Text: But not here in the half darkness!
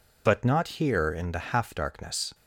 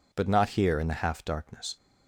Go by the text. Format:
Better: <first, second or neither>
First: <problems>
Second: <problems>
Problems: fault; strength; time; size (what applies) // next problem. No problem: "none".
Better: neither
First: none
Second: none